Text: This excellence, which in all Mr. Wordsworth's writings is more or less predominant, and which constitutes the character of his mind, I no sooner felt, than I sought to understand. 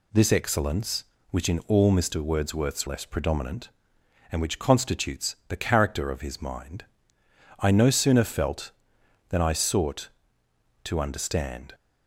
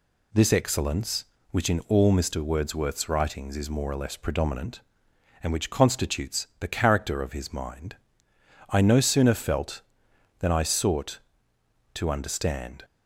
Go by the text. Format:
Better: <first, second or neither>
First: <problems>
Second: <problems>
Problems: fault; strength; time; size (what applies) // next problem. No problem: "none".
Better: second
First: skips "writings is more or"; at 2.8 s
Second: none